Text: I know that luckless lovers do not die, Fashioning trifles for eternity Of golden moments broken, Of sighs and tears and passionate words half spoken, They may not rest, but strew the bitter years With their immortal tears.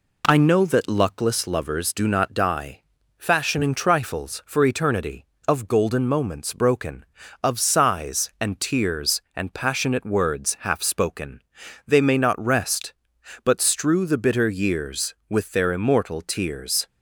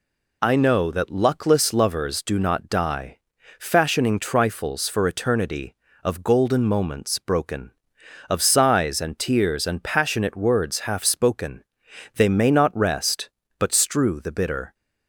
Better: first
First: none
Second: stops before "years With their immortal tears"; at 14.7 s

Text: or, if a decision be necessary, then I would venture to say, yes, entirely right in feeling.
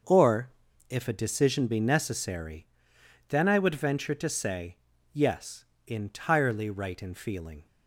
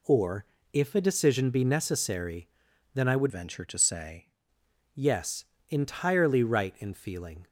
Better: first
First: none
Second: changes voice from "venture" to "say"; from 3.3 to 4.3 s; 1.0 s long

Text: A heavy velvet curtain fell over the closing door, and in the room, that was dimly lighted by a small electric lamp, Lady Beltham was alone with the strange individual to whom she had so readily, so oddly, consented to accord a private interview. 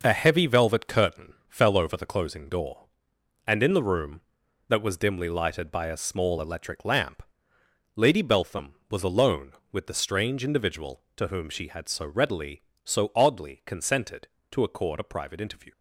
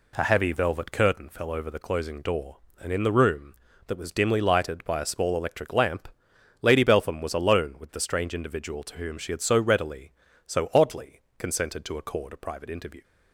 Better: neither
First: none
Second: none

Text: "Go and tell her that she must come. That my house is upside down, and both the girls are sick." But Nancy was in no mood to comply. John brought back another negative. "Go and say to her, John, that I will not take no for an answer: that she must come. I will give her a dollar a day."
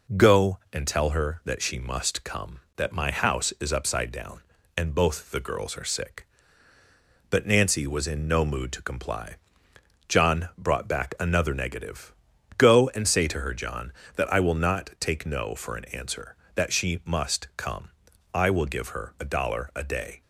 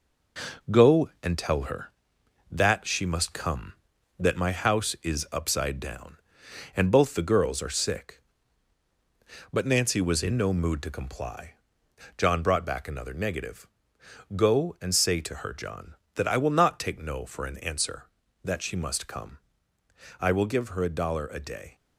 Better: first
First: none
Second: gets quieter; noticeable; throughout; 5 dB

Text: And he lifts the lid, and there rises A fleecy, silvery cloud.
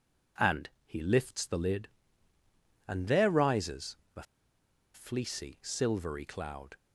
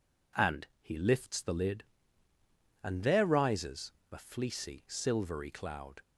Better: second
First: pauses between "And" and "he"; slight; at 0.6 s; 0.16 s long // pauses between "rises" and "A"; slight; at 3.9 s; 0.18 s long // pauses between "A" and "fleecy"; noticeable; at 4.2 s; 0.71 s long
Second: pauses between "rises" and "A"; slight; at 3.9 s; 0.18 s long

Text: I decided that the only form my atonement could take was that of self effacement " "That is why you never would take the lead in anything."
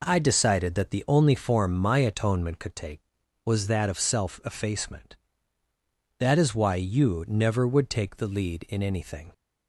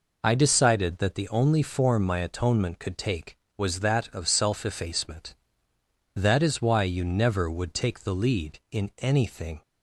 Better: neither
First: none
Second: none

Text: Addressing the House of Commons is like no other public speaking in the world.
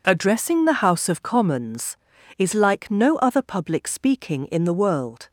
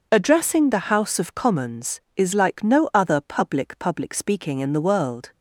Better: first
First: none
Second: says "public" twice; at 3.7 s

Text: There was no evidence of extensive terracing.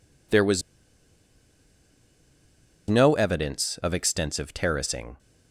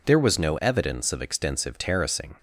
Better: second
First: pauses between "was" and "no"; strong; at 0.6 s; 2.2 s long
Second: none

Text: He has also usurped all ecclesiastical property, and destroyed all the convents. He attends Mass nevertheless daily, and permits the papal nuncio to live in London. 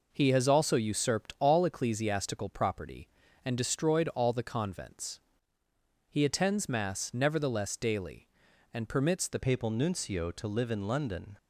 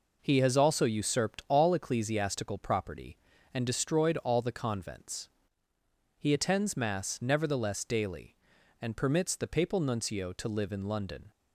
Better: second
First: changes voice at "papal"; from 9.3 s on; 2.0 s long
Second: none

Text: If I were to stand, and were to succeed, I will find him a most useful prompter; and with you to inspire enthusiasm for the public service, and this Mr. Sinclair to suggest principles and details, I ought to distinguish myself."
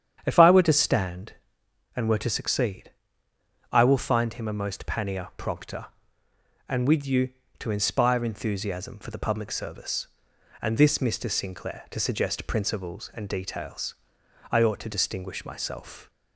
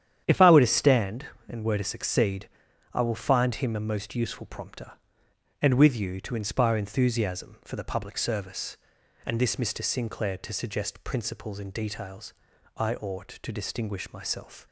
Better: second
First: starts louder than the rest; strong; until 1.2 s; 9 dB // says "pannier" for "useful"; at 4.8 s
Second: starts louder than the rest; strong; until 1.2 s; 9.5 dB

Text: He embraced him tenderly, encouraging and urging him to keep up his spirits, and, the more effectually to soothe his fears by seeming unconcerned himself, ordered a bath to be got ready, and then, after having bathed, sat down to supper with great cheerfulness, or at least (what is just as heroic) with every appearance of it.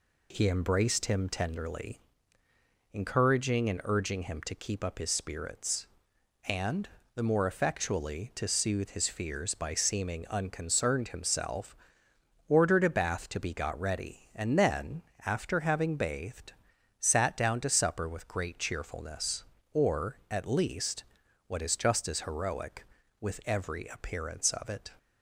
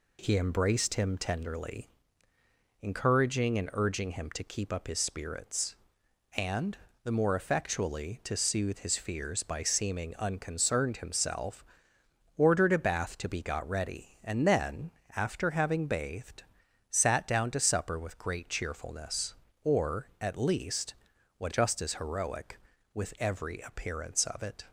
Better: first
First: none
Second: skips "is"; at 21.5 s

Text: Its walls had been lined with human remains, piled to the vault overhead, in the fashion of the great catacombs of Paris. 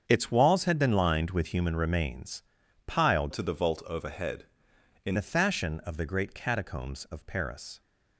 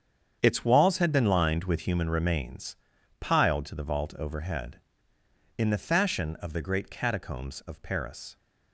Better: second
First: starts louder than the rest; strong; until 1.0 s; 7.5 dB // changes voice from "to" to "in"; from 3.3 to 5.1 s; 1.8 s long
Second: starts louder than the rest; strong; until 1.4 s; 8 dB

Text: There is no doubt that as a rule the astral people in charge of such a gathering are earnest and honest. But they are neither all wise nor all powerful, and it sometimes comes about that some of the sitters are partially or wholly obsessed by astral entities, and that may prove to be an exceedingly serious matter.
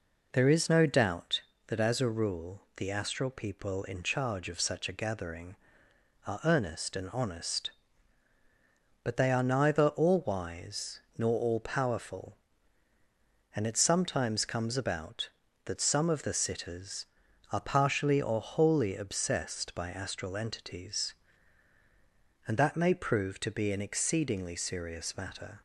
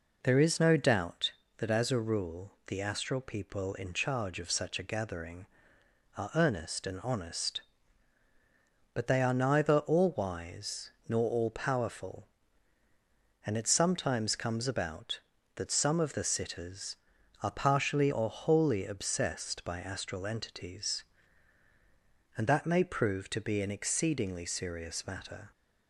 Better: neither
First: pauses between "wise" and "nor"; slight; at 11.0 s; 0.16 s long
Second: pauses between "wise" and "nor"; slight; at 10.9 s; 0.16 s long

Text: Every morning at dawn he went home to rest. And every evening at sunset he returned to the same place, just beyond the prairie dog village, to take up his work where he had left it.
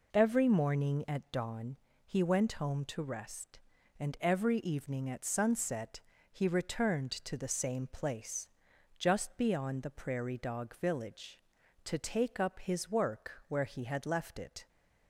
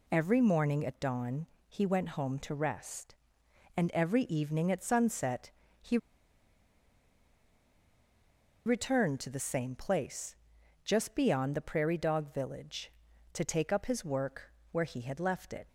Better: first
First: pauses between "dawn" and "he"; slight; at 1.7 s; 0.28 s long // pauses between "sunset" and "he"; slight; at 6.0 s; 0.32 s long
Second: pauses between "dawn" and "he"; slight; at 1.4 s; 0.20 s long // pauses between "sunset" and "he"; slight; at 5.5 s; 0.30 s long // pauses between "he" and "returned"; strong; at 5.9 s; 2.6 s long // pauses between "work" and "where"; slight; at 14.5 s; 0.20 s long

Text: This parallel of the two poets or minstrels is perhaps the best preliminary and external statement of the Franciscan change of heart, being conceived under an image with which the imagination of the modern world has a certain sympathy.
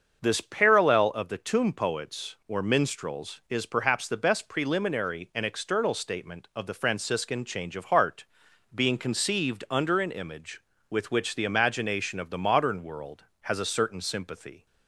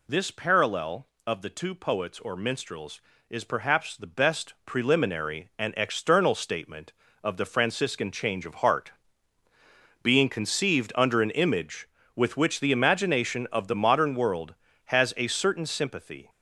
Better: second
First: starts louder than the rest; until 1.2 s; 6.5 dB // says "tomb" for "two"; at 1.3 s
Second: none

